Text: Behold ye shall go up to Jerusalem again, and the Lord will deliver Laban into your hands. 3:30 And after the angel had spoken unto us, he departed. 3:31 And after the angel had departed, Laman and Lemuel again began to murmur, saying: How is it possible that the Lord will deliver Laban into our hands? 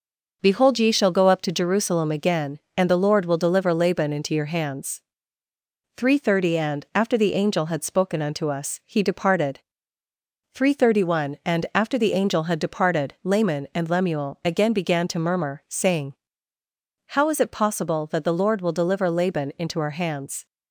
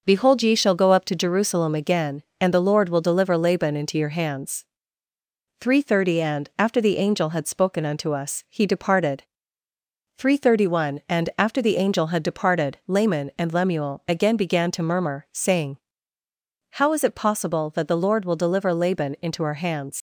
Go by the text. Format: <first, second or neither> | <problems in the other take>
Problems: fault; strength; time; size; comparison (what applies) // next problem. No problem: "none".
first | leaves "hands" unfinished; at 19.9 s; 90 ms